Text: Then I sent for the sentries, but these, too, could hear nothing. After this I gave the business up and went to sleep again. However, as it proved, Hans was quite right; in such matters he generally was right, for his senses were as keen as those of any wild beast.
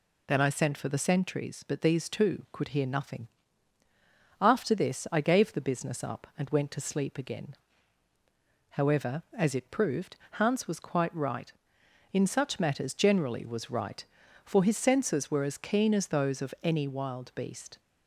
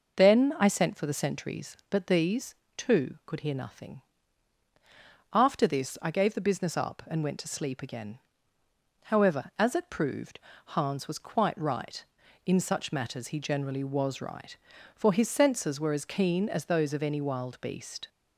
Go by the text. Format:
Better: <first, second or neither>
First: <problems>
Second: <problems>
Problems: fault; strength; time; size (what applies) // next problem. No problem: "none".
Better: second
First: skips "he"; at 12.9 s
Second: none